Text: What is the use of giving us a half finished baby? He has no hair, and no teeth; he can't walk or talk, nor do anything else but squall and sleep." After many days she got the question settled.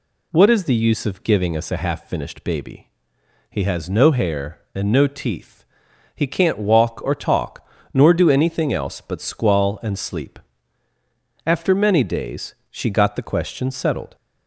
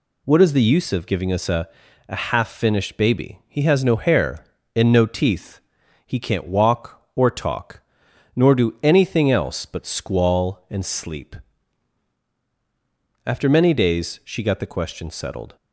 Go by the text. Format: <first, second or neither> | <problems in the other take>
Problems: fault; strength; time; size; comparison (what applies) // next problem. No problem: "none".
first | says "a" twice; at 2.0 s